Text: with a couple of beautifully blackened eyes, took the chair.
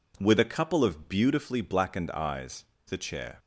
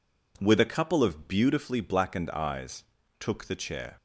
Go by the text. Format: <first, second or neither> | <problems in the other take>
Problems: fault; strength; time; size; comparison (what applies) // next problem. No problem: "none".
second | skips "took"; at 2.7 s